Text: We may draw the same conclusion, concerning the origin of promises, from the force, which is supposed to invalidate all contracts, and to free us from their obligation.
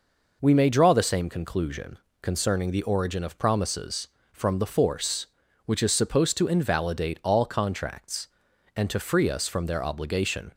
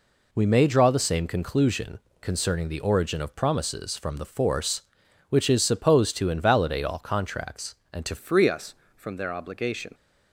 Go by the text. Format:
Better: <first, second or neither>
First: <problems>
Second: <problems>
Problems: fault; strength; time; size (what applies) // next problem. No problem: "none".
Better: first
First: none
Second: changes voice at "free"; from 8.1 s on; 1.8 s long